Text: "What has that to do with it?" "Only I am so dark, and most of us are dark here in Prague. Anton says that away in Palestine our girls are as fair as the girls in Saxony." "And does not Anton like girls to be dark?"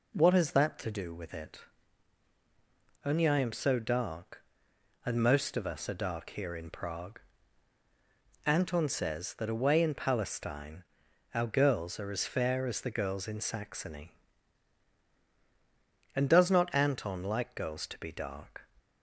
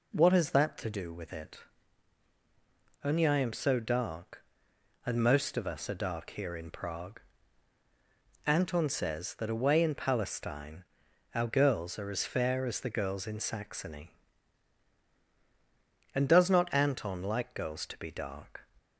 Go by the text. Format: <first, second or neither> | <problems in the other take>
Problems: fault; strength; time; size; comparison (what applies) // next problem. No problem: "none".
neither | pauses between "Palestine" and "our"; noticeable; the same in both